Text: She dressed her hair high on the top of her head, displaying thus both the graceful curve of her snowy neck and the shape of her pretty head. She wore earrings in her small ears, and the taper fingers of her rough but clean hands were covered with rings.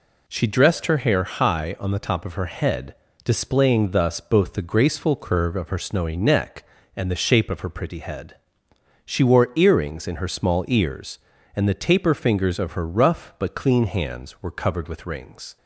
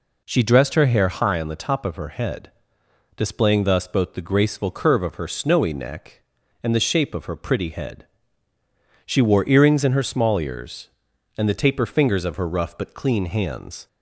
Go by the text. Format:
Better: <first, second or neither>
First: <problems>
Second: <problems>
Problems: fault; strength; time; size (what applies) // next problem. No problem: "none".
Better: first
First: none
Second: stops before "were covered with rings"; at 13.8 s